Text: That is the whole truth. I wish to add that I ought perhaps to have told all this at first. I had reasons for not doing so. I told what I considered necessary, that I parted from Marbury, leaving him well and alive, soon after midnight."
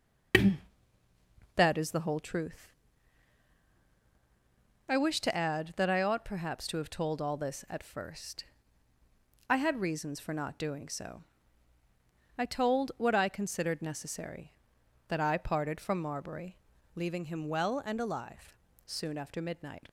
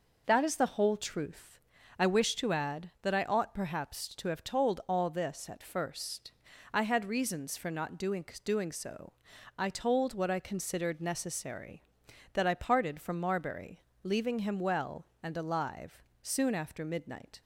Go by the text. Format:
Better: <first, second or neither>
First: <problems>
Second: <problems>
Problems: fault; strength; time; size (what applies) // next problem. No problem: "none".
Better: first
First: none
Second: says "doing" twice; at 8.4 s